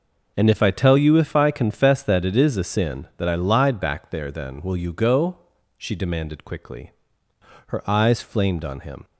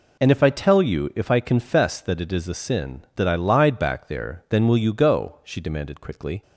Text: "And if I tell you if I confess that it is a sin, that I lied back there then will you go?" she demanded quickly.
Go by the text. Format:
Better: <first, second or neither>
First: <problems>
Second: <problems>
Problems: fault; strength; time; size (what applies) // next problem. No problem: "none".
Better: second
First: goes on to say "Her eyes flamed on him"; from 7.6 s on; 1.3 s long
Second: none